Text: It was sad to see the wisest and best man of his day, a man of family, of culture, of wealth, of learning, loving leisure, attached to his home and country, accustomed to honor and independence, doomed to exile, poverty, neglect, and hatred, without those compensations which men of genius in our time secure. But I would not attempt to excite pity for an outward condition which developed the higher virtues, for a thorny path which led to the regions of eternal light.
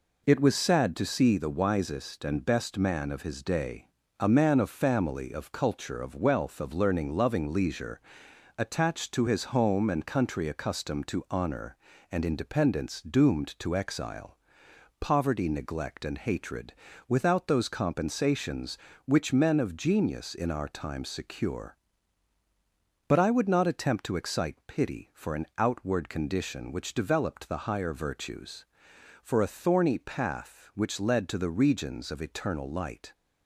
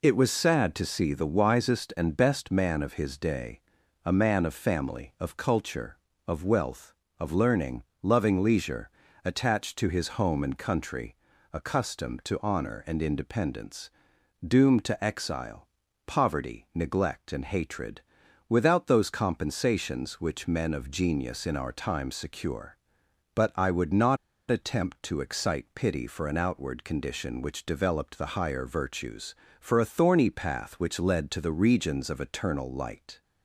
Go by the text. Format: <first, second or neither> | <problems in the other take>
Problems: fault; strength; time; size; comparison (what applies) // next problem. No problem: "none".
first | pauses between "not" and "attempt"; slight; at 24.1 s; 0.32 s long